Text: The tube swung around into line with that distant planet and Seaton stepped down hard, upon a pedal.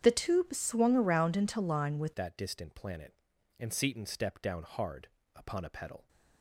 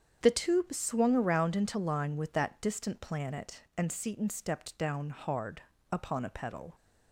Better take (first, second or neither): second